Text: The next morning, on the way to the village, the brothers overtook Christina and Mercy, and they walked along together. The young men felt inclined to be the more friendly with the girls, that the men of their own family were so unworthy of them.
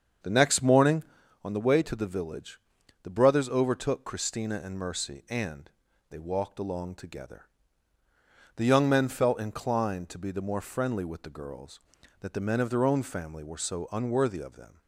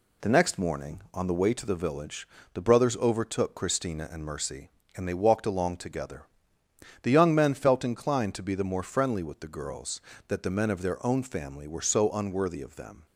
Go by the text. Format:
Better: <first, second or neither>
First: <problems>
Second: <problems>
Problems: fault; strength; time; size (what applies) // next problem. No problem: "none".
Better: second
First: starts louder than the rest; until 1.5 s; 7 dB // pauses between "and" and "they"; at 5.7 s; 0.40 s long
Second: none